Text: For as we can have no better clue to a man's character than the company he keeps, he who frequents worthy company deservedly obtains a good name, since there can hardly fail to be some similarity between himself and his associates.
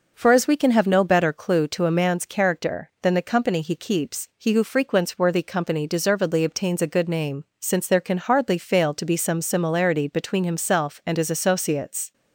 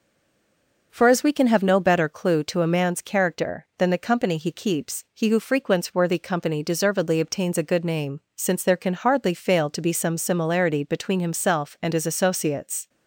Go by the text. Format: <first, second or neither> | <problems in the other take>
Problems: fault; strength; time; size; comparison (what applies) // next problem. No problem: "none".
first | stays silent before the first word; slight; until 0.9 s; 0.9 s long